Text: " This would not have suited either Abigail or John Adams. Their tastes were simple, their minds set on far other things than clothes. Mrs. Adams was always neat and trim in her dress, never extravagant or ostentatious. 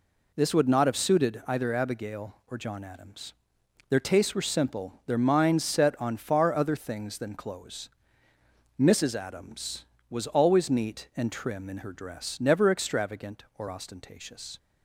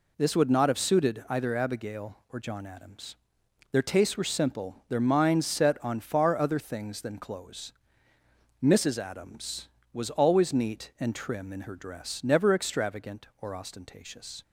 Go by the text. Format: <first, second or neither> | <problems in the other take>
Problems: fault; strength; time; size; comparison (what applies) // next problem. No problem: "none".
neither | none